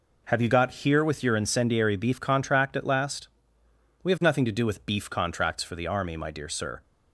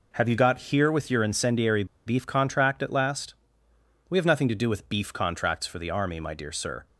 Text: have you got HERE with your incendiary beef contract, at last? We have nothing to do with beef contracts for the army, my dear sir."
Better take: first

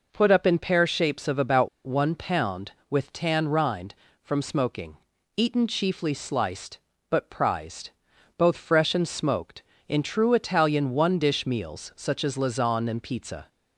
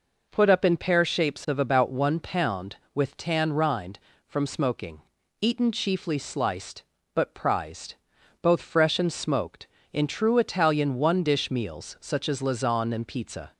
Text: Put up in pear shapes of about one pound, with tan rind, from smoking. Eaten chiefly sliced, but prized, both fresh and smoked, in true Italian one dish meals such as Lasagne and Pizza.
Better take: second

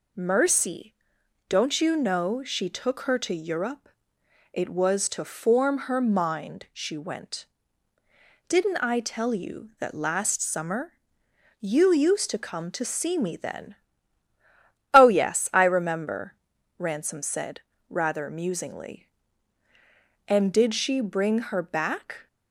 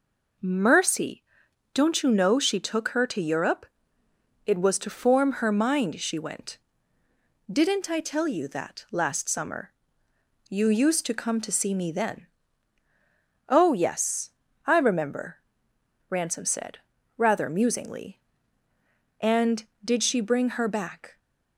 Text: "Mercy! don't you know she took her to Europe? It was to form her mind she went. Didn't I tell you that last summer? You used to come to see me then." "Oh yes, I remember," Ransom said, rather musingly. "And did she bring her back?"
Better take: neither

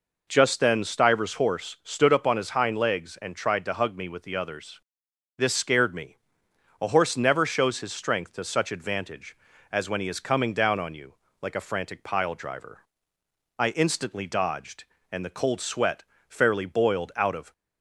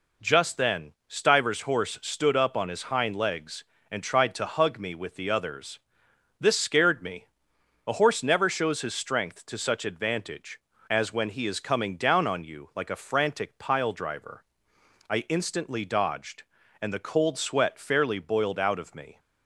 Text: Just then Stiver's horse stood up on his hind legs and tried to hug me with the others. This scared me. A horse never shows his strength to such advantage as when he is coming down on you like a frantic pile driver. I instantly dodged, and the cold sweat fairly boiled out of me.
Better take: second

